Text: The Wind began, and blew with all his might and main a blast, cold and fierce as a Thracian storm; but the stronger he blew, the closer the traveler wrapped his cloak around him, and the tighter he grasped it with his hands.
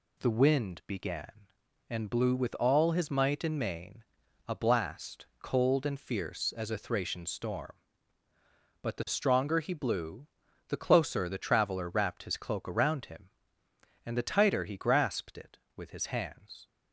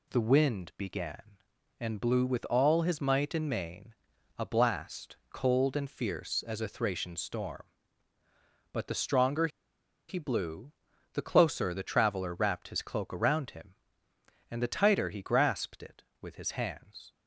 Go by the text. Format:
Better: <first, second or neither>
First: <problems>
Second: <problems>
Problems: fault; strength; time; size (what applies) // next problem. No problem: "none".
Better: first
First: pauses between "main" and "a"; at 4.0 s; 0.44 s long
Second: pauses between "main" and "a"; at 3.9 s; 0.44 s long // pauses between "stronger" and "he"; noticeable; at 9.4 s; 0.61 s long